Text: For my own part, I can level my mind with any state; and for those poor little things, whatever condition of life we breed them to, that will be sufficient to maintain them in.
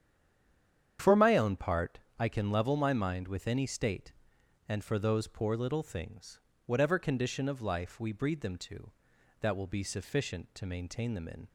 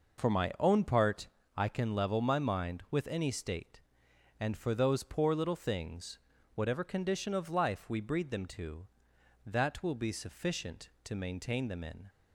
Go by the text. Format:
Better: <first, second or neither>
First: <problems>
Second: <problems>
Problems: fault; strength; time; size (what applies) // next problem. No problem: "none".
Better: second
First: stays silent before the first word; until 0.9 s; 0.9 s long // starts louder than the rest; strong; until 2.2 s; 9 dB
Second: none